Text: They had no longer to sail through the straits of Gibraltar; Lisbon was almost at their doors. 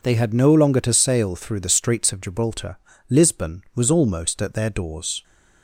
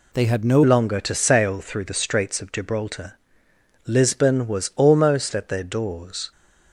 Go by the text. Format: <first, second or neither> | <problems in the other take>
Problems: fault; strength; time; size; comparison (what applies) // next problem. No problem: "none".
first | changes voice at "longer"; from 0.6 s on; 5.7 s long